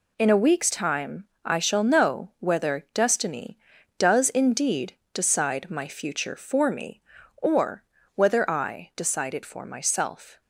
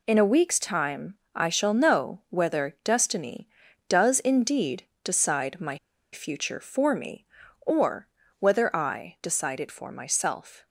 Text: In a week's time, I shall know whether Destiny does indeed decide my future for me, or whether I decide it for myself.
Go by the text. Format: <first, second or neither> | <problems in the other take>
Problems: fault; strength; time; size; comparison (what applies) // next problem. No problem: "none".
first | pauses between "indeed" and "decide"; slight; at 4.8 s; 0.22 s long; slight in the first // pauses between "my" and "future"; slight; at 5.7 s; 0.36 s long // pauses between "or" and "whether"; slight; at 8.0 s; 0.32 s long; slight in the first